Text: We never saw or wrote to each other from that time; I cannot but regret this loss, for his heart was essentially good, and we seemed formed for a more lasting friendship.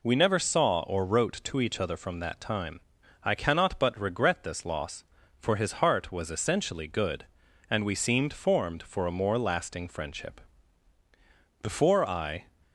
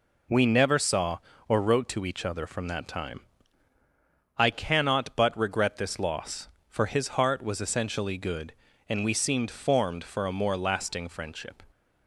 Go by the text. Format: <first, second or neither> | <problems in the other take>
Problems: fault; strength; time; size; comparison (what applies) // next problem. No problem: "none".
second | goes on to say "Before I"; noticeable; from 11.6 s on; 0.84 s long